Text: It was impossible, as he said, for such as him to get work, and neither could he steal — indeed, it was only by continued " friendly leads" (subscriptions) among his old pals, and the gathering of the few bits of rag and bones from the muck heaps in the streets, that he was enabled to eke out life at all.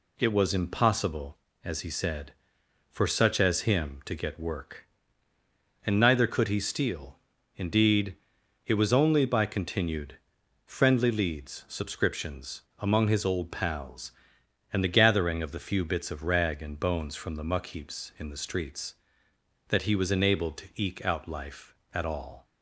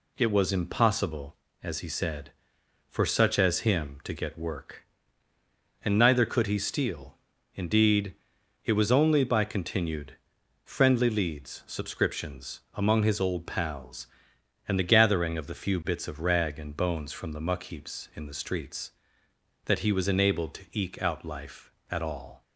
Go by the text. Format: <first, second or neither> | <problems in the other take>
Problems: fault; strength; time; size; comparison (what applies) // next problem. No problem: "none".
neither | none